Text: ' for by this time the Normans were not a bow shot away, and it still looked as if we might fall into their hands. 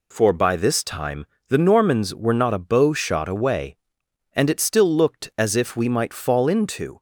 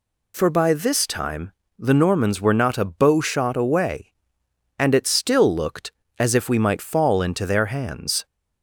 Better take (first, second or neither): second